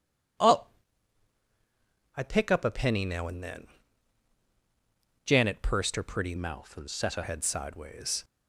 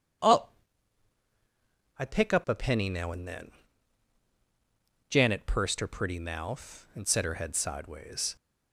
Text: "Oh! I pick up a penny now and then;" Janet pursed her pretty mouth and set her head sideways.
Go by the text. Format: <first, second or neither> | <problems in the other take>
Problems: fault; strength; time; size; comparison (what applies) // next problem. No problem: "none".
second | changes voice from "mouth" to "her"; from 6.3 to 7.2 s; 0.9 s long